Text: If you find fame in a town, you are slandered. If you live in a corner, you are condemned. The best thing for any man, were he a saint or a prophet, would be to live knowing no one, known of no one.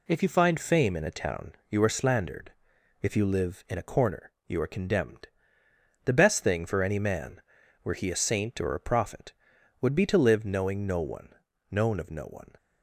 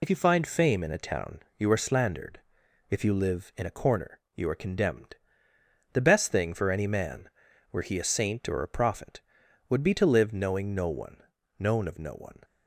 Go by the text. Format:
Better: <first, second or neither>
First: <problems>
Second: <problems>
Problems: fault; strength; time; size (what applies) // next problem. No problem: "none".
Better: first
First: none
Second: loses the start of "If"; at 0.0 s; 55 ms